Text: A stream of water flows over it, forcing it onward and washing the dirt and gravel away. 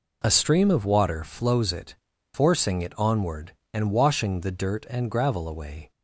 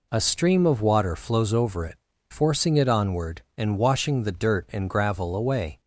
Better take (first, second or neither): second